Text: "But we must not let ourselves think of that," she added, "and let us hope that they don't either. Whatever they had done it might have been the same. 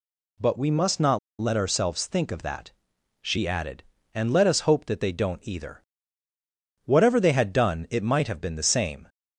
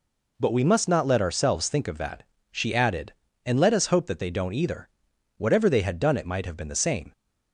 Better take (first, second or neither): second